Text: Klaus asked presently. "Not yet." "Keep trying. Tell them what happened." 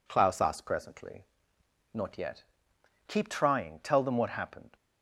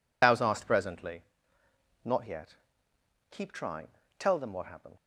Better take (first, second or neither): first